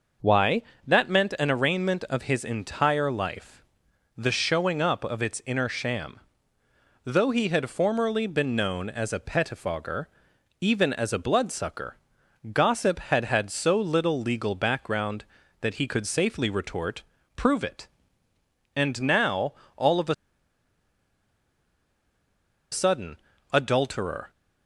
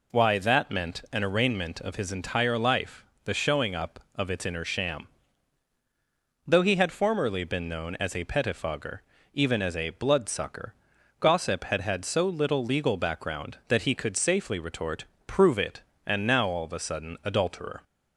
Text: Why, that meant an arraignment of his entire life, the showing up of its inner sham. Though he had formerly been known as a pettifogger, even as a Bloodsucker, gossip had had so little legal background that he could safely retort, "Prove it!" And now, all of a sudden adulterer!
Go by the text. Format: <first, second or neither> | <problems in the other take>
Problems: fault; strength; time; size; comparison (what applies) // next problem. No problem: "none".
second | pauses between "a" and "sudden"; strong; at 20.1 s; 2.5 s long // pauses between "sudden" and "adulterer"; slight; at 23.1 s; 0.36 s long